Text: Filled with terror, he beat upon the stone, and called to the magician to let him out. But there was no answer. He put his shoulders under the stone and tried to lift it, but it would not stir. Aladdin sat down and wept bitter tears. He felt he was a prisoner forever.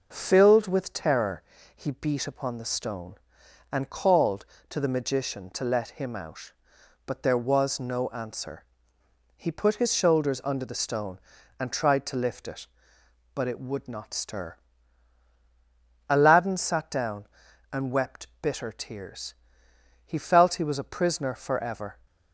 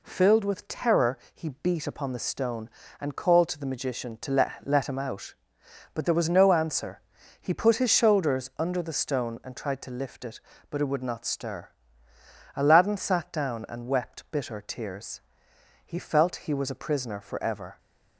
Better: first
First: none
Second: says "let" twice; at 4.6 s

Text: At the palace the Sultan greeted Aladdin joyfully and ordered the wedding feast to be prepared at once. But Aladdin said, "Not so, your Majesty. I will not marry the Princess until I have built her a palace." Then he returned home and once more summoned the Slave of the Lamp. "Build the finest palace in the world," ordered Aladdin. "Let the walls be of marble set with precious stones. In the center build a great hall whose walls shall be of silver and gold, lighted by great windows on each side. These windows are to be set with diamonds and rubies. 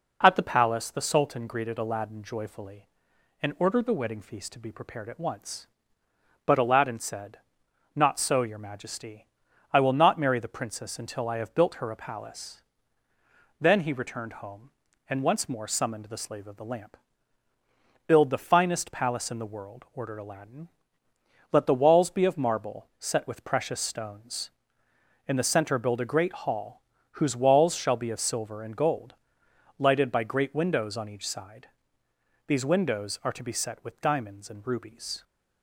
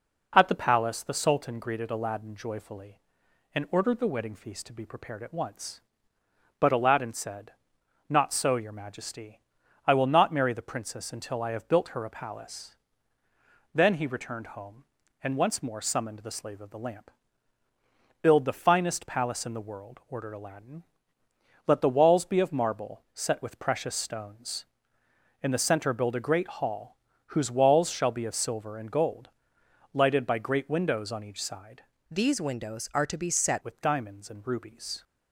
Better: first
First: pauses between "hall" and "whose"; slight; at 26.8 s; 0.30 s long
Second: pauses between "hall" and "whose"; slight; at 26.9 s; 0.30 s long // changes voice from "These" to "set"; from 32.0 to 33.6 s; 1.6 s long

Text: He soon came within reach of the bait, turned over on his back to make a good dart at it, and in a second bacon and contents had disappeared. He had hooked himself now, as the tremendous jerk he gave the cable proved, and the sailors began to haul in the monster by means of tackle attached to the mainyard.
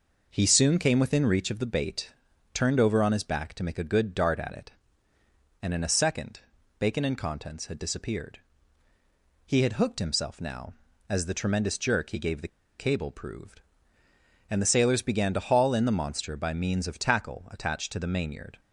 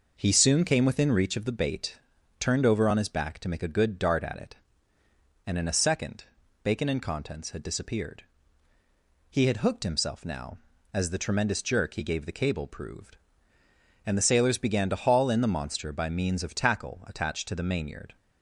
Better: second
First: pauses between "second" and "bacon"; at 6.3 s; 0.40 s long // pauses between "the" and "cable"; slight; at 12.4 s; 0.31 s long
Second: pauses between "second" and "bacon"; at 6.2 s; 0.40 s long

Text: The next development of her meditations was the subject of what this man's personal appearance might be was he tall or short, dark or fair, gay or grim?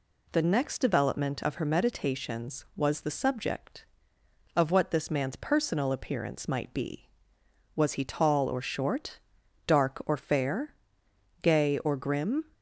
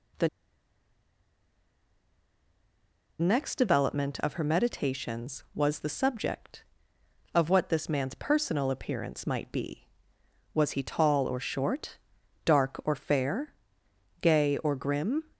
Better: first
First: none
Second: pauses between "The" and "next"; strong; at 0.2 s; 2.9 s long

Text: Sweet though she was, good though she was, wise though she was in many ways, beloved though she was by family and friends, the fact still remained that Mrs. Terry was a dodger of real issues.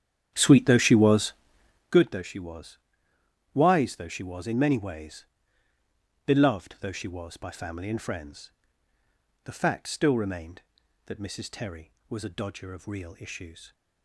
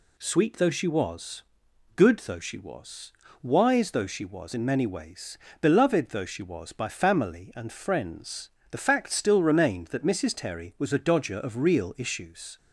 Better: second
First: starts louder than the rest; strong; until 2.0 s; 9.5 dB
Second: none

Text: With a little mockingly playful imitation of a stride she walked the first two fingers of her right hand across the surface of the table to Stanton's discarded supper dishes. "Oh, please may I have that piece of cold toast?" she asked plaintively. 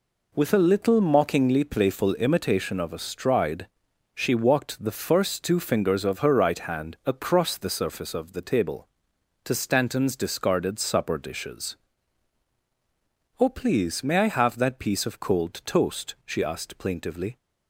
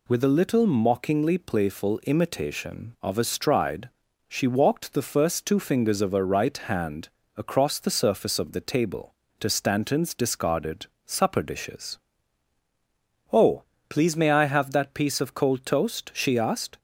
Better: first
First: pauses between "stride" and "she"; noticeable; at 3.6 s; 0.48 s long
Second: pauses between "stride" and "she"; at 3.8 s; 0.38 s long // pauses between "hand" and "across"; slight; at 7.0 s; 0.28 s long // pauses between "discarded" and "supper"; slight; at 10.8 s; 0.20 s long // stops before "plaintively"; at 16.7 s

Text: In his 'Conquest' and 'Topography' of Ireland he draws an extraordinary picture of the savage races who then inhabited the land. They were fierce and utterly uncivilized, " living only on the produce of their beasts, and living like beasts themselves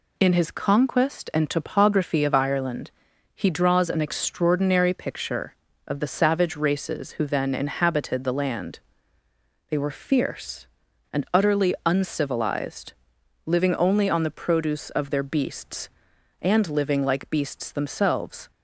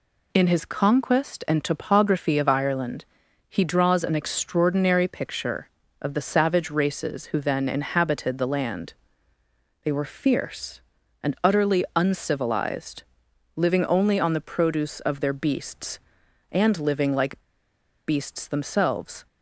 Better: first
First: pauses between "Ireland" and "he"; at 2.9 s; 0.44 s long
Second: pauses between "Ireland" and "he"; at 3.0 s; 0.44 s long // pauses between "like" and "beasts"; noticeable; at 17.4 s; 0.66 s long

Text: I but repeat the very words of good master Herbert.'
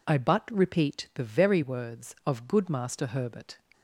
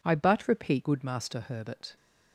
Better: first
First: none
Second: skips "the very words of"; at 0.8 s

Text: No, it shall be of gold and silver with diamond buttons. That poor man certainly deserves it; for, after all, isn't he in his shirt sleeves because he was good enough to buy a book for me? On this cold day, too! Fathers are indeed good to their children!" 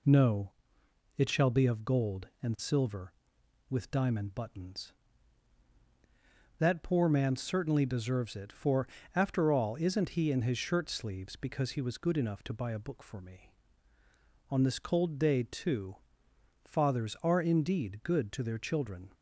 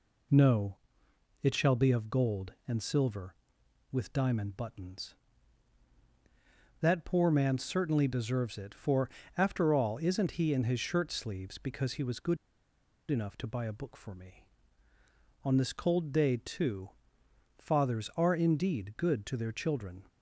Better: first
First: none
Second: pauses between "good" and "enough"; noticeable; at 12.3 s; 0.73 s long

